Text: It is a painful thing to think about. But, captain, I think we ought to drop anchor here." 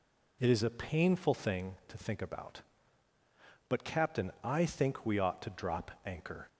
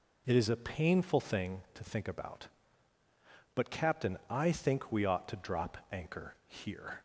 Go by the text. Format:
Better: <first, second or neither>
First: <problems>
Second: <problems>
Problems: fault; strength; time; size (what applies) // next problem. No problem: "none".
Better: second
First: stops before "here"; at 6.4 s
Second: none